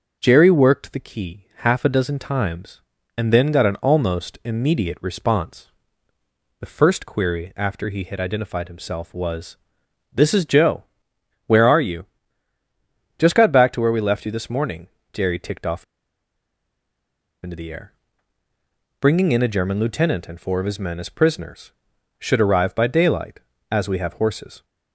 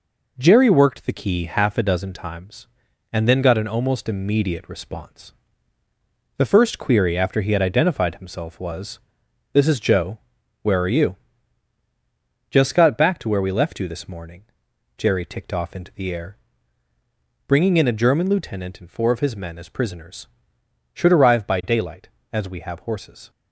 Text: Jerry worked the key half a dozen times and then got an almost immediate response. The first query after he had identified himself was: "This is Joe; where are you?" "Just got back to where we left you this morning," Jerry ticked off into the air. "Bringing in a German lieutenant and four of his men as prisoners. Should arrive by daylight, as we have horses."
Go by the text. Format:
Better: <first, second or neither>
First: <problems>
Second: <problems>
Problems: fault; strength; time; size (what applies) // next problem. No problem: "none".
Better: second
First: starts louder than the rest; until 1.2 s; 6.5 dB // pauses between "off" and "into"; strong; at 15.8 s; 1.5 s long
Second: none